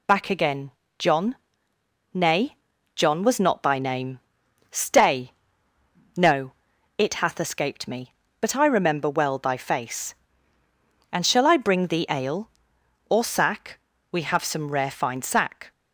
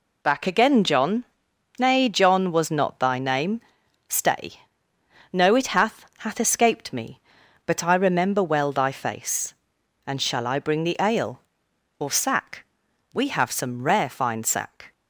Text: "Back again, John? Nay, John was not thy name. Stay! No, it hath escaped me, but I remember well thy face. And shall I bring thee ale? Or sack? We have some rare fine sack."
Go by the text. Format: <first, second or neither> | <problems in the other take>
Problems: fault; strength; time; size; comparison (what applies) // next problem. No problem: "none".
first | says "hath" twice; at 6.1 s